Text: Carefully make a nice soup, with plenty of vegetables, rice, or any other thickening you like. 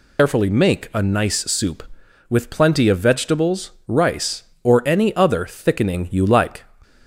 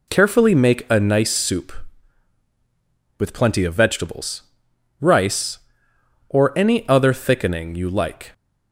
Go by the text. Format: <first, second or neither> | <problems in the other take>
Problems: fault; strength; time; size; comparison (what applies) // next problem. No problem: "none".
second | loses the start of "Carefully"; at 0.1 s; 110 ms